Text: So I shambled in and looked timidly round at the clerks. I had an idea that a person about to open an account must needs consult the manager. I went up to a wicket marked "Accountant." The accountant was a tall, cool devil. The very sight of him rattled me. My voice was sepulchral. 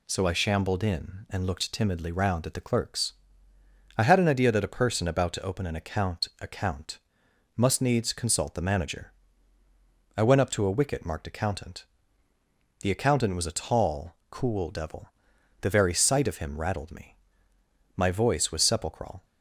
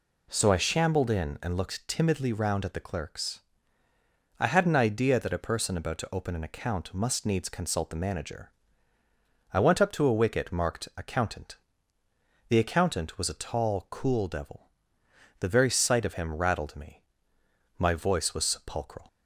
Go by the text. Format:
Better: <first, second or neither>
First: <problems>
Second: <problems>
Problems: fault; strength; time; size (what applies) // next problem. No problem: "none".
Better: second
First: says "account" twice; at 6.3 s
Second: none